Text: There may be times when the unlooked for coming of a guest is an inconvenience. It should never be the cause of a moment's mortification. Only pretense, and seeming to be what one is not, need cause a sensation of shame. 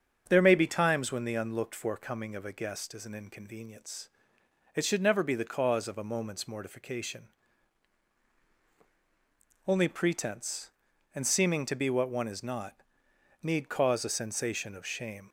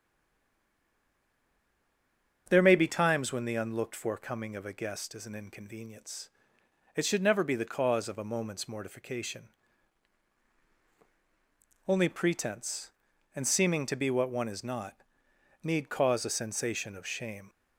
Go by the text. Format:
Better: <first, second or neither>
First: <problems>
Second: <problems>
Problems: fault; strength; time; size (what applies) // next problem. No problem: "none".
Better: first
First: starts louder than the rest; strong; until 1.2 s; 7 dB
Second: stays silent before the first word; until 2.4 s; 2.4 s long // starts louder than the rest; strong; until 3.5 s; 7 dB